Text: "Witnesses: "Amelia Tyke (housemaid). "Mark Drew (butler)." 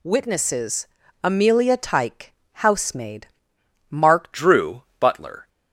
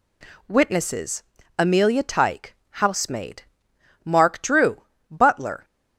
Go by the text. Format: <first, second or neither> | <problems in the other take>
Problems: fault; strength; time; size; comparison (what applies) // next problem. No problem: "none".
second | changes voice at "Drew"; from 4.3 s on; 1.1 s long